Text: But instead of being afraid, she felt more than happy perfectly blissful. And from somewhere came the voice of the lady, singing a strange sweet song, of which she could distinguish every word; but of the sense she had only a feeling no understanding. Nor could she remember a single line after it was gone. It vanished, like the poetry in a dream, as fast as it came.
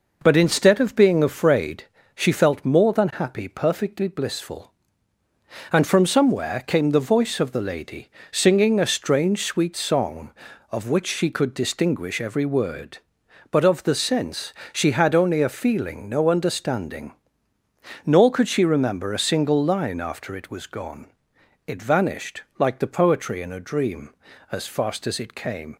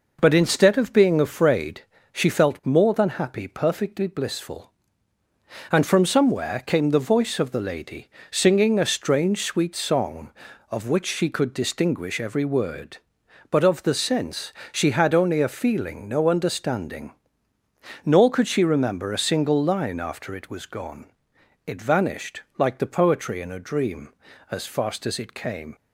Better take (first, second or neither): neither